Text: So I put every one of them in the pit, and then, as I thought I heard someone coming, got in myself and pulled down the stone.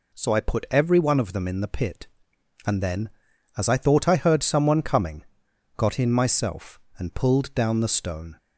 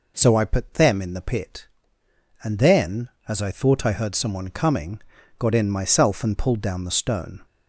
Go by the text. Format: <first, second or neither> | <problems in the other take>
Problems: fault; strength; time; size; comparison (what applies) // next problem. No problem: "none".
first | skips "every one of"; at 0.7 s